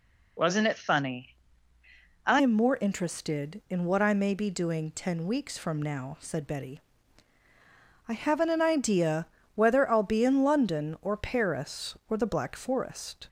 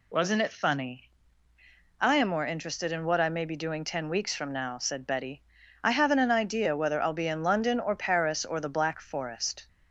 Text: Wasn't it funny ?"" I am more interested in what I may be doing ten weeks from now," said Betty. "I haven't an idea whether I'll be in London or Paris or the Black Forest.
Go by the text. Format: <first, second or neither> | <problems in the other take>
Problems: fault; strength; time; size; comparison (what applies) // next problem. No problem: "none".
second | changes voice at "am"; from 2.3 s on; 10.9 s long // pauses between "idea" and "whether"; slight; at 9.2 s; 0.26 s long